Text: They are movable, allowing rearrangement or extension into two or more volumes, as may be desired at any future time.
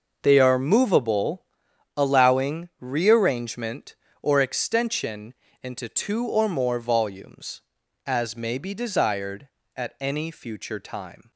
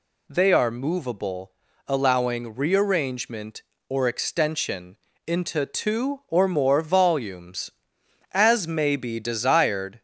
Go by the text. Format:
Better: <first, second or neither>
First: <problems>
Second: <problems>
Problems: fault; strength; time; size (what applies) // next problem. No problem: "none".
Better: first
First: pauses between "extension" and "into"; slight; at 5.3 s; 0.30 s long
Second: pauses between "extension" and "into"; slight; at 4.9 s; 0.28 s long // stops before "at any future time"; at 9.9 s